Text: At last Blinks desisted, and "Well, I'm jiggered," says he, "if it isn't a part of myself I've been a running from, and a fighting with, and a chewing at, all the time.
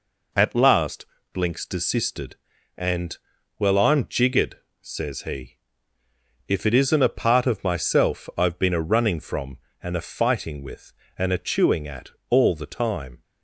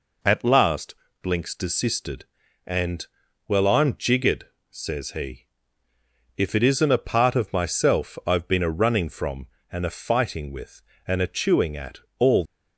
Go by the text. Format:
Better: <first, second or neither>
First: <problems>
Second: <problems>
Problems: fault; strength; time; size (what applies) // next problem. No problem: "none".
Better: first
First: pauses between "last" and "Blinks"; slight; at 1.0 s; 0.26 s long // pauses between "and" and "Well"; at 3.1 s; 0.40 s long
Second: pauses between "last" and "Blinks"; slight; at 0.9 s; 0.26 s long // pauses between "and" and "Well"; at 3.0 s; 0.40 s long // stops before "the time"; at 12.4 s